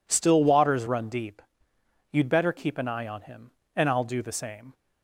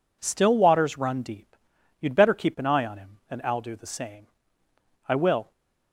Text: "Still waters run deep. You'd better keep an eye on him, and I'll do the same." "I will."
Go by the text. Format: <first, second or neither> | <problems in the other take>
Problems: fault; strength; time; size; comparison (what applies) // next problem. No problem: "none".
second | stops before "I will"; at 4.7 s